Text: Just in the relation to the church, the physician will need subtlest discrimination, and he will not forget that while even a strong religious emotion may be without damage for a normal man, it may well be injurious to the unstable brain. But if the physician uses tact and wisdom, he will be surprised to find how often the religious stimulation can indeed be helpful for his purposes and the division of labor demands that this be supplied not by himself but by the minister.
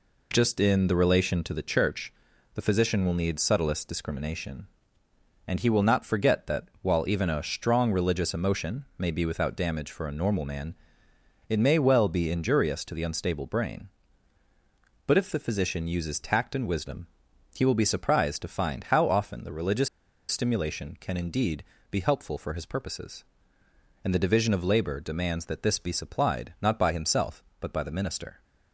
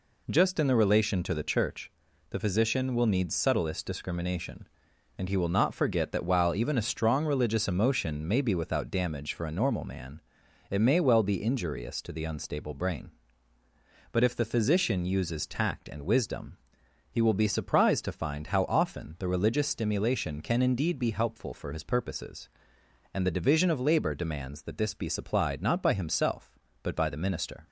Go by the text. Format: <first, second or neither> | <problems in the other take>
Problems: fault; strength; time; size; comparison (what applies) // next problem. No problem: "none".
second | pauses between "religious" and "stimulation"; at 19.8 s; 0.42 s long // pauses between "indeed" and "be"; slight; at 21.6 s; 0.28 s long